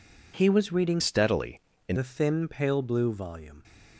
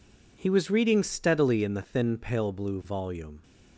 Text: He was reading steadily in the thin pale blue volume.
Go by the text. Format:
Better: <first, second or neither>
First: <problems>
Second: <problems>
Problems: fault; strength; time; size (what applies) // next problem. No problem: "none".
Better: second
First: changes voice from "steadily" to "in"; from 0.9 to 1.9 s; 1.0 s long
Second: none